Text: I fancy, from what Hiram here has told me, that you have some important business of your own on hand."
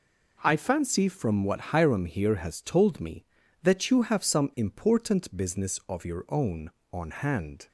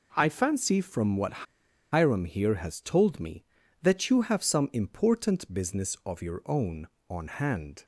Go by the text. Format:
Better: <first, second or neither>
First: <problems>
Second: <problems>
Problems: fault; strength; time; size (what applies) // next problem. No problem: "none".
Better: first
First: none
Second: pauses between "what" and "Hiram"; noticeable; at 1.4 s; 0.47 s long